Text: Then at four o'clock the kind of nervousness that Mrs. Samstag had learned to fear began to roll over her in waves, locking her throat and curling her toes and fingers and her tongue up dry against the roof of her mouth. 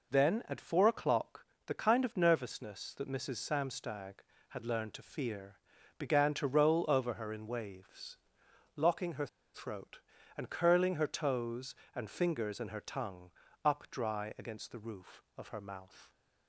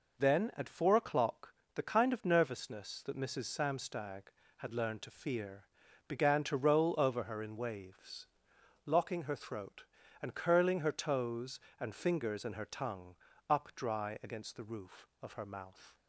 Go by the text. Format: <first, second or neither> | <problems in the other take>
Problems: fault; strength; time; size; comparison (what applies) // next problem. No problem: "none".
second | pauses between "o'clock" and "the"; slight; at 1.4 s; 0.22 s long; slight in the second // pauses between "fear" and "began"; at 5.5 s; 0.40 s long; also in the second // pauses between "her" and "throat"; slight; at 9.2 s; 0.27 s long // pauses between "tongue" and "up"; slight; at 13.3 s; 0.34 s long; slight in the second